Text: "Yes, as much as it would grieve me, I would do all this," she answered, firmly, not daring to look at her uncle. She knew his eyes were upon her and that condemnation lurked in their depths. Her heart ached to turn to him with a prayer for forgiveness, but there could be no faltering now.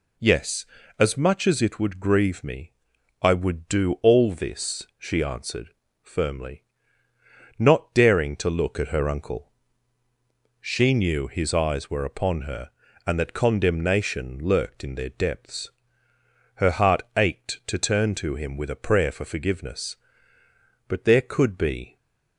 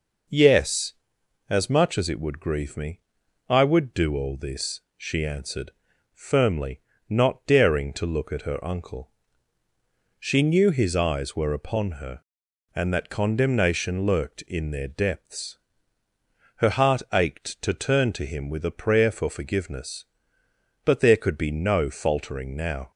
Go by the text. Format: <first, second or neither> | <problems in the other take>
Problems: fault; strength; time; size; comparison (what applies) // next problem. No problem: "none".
second | stays silent after the last word; slight; from 21.8 s on; 0.5 s long // stops before "no faltering now"; at 21.9 s